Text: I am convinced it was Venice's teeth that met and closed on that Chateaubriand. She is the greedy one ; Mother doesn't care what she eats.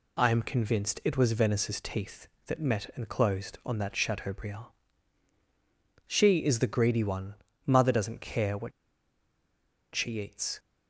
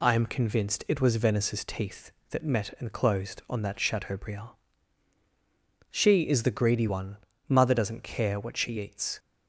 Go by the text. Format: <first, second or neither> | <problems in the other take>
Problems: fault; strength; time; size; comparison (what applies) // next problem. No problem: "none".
second | pauses between "what" and "she"; at 8.7 s; 1.2 s long